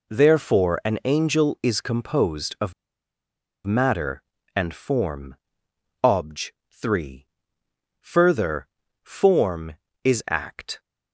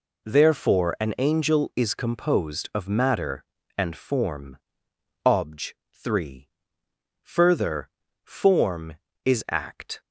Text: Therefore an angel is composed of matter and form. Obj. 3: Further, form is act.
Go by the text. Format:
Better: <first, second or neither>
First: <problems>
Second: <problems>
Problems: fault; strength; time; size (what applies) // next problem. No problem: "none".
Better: second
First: pauses between "of" and "matter"; noticeable; at 2.7 s; 0.94 s long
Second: none